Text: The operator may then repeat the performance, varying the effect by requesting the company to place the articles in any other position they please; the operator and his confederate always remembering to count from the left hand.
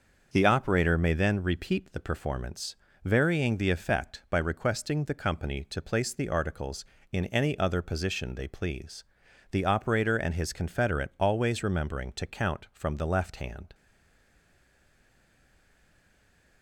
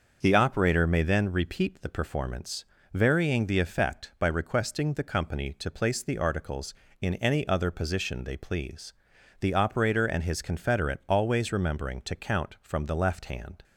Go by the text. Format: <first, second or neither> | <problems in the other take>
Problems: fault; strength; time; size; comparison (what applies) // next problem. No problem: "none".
second | starts louder than the rest; until 1.3 s; 6.5 dB; also in the second // stays silent after the last word; strong; from 13.7 s on; 2.9 s long